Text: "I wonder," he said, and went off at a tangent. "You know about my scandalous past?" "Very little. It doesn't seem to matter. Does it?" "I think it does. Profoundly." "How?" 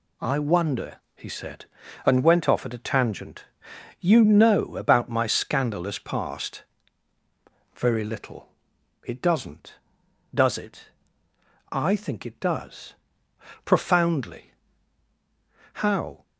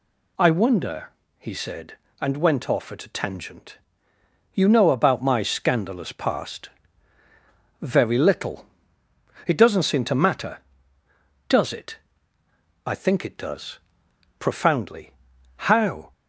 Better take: second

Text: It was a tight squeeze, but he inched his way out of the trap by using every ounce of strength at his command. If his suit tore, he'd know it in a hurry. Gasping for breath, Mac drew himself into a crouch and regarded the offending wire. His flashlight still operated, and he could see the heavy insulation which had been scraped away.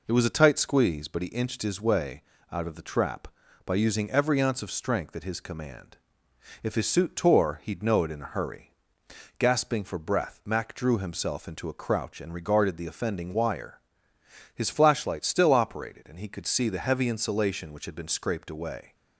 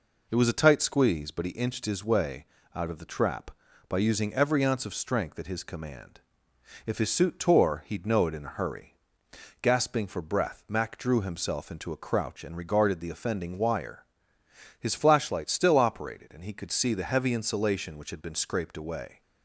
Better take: neither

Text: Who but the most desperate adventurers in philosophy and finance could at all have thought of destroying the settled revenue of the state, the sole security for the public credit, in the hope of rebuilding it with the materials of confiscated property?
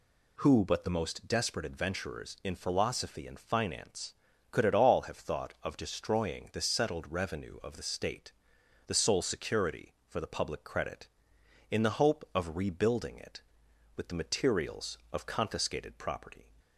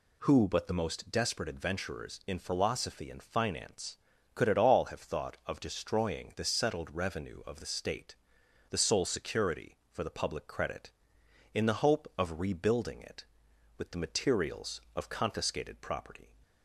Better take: neither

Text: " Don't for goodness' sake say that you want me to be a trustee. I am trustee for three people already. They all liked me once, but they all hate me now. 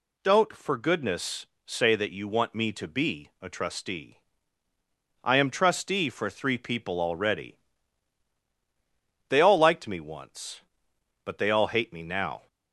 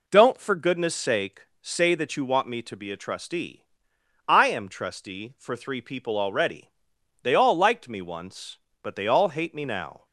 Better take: second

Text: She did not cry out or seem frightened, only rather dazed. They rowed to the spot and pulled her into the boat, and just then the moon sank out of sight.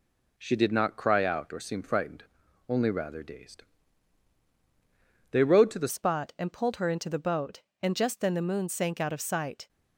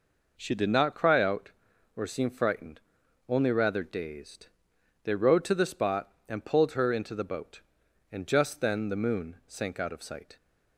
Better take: second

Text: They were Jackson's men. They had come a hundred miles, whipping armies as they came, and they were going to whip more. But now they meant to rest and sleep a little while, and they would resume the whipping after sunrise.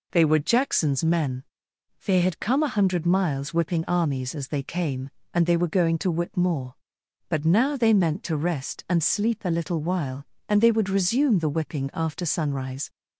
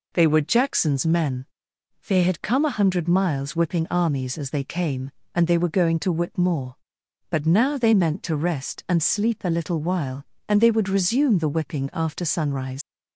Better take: first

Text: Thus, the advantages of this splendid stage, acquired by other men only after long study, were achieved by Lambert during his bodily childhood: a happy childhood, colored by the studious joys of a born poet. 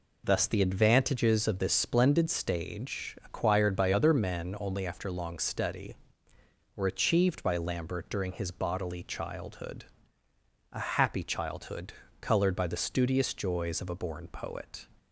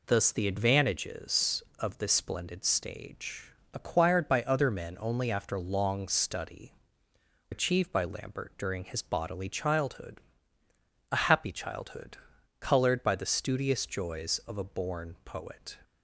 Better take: first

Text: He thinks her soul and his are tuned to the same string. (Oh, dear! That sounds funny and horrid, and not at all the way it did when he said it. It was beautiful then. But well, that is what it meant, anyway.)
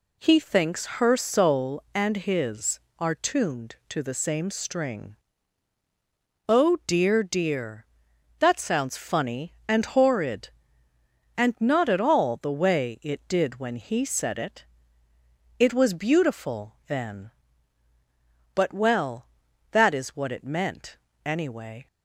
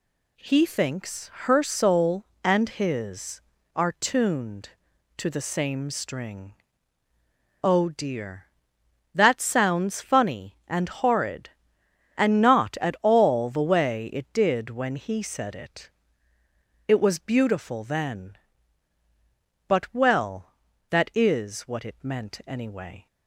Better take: second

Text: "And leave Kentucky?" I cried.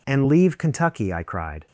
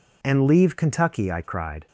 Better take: neither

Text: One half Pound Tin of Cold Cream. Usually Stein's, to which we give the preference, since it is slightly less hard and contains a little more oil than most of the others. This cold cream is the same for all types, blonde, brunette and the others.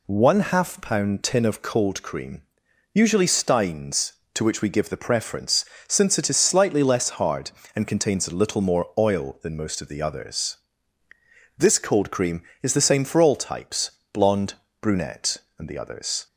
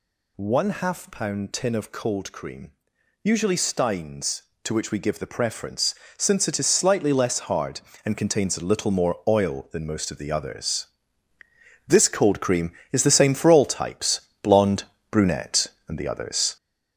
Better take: first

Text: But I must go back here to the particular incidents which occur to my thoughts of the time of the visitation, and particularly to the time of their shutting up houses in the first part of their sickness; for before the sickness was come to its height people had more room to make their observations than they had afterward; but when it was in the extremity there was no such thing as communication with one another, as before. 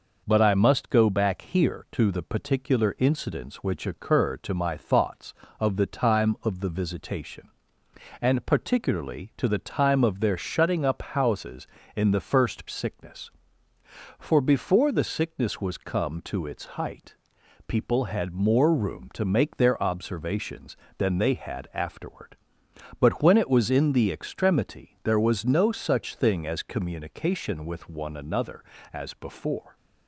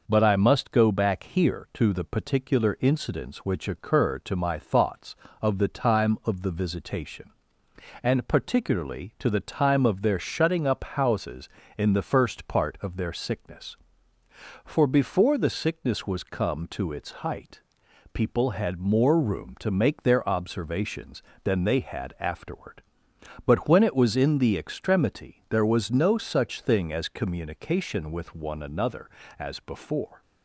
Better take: second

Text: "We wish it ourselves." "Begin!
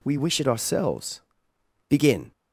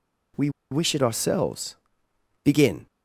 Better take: first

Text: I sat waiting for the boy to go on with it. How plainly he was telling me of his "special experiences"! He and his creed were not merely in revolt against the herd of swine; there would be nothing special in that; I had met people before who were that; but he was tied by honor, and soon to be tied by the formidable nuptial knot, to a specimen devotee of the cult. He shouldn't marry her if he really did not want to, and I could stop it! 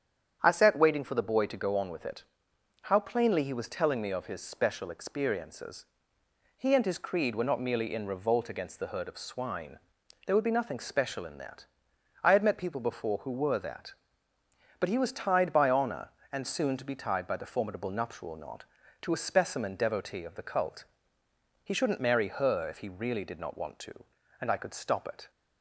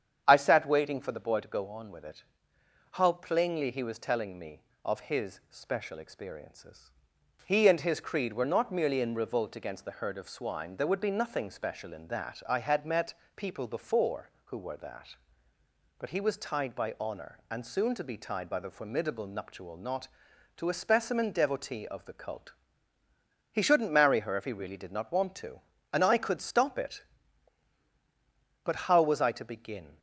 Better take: first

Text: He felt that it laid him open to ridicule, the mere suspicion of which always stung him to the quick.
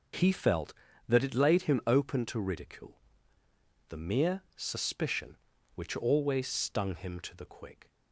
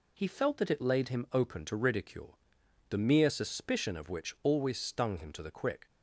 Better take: second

